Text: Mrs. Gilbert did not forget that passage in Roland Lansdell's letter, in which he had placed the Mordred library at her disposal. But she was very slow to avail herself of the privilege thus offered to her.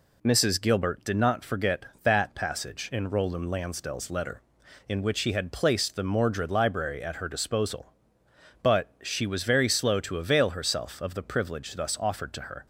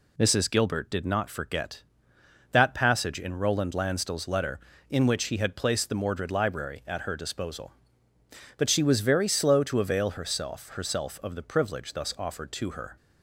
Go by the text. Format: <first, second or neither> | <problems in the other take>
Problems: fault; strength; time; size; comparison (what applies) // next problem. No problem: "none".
first | says "herself" twice; at 10.6 s